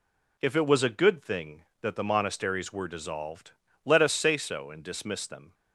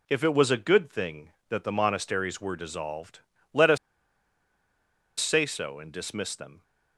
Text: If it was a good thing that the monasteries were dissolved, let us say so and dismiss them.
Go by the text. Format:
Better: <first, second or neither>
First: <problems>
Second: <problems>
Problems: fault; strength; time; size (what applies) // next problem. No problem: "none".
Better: first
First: none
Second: pauses between "us" and "say"; strong; at 3.7 s; 1.4 s long